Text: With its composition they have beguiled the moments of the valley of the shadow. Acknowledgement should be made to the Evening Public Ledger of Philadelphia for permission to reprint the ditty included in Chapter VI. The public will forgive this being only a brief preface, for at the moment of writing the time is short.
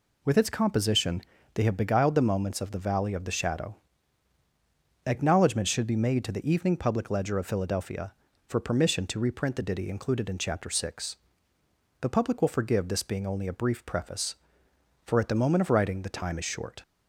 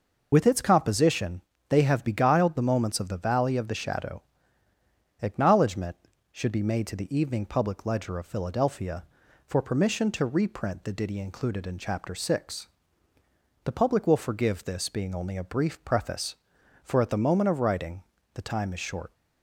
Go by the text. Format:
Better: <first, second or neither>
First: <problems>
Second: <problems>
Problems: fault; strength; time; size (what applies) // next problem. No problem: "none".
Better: first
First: pauses between "composition" and "they"; slight; at 1.2 s; 0.32 s long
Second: loses the start of "With"; at 0.3 s; 40 ms // pauses between "composition" and "they"; slight; at 1.4 s; 0.26 s long // pauses between "writing" and "the"; slight; at 18.0 s; 0.32 s long